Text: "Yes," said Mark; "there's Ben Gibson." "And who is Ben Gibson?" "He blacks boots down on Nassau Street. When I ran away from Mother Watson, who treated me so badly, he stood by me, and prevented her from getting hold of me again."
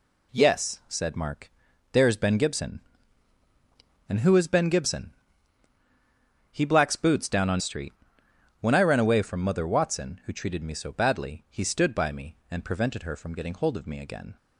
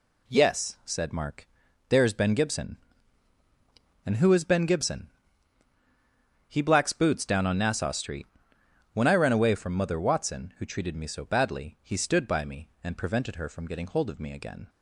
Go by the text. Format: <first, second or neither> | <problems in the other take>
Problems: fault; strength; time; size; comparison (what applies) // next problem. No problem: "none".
second | skips "Nassau"; at 7.5 s